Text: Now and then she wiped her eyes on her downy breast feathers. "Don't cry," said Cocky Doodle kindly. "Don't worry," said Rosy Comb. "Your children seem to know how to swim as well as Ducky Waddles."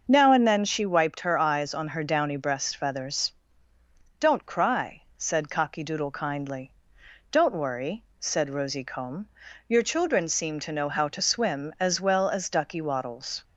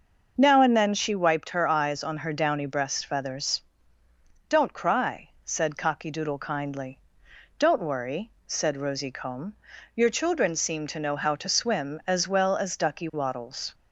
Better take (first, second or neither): neither